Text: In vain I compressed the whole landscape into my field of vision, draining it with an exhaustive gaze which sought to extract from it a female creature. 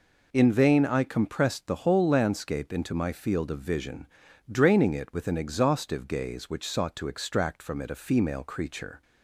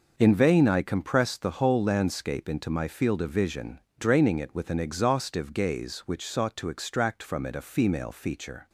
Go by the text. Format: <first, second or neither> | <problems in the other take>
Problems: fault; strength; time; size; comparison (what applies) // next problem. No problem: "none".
first | says "feature" for "creature"; at 8.1 s